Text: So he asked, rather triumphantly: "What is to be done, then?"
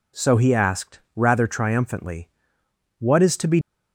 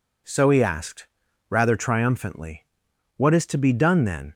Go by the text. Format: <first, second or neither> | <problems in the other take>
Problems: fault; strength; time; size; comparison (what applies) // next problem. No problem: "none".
second | stops before "done then"; at 3.6 s